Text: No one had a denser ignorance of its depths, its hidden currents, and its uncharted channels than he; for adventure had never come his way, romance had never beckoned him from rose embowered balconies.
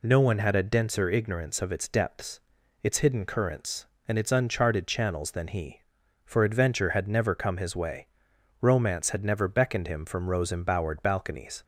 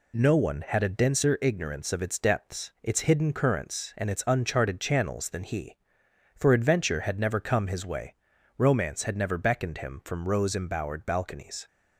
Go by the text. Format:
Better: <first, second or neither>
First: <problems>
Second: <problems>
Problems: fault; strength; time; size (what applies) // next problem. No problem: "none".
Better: neither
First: none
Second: none